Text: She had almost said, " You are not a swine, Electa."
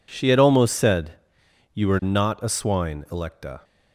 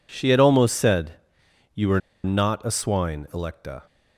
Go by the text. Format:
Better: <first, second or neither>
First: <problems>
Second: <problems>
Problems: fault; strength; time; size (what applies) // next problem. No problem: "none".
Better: first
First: none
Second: pauses between "are" and "not"; slight; at 1.9 s; 0.24 s long